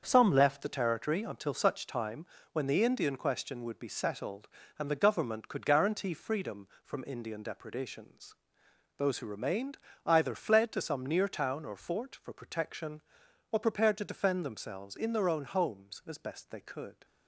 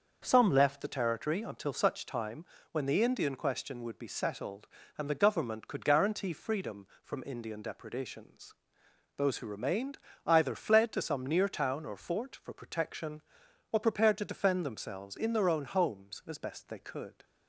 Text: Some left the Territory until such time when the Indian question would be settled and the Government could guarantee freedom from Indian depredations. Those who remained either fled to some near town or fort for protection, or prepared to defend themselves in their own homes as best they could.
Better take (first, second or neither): second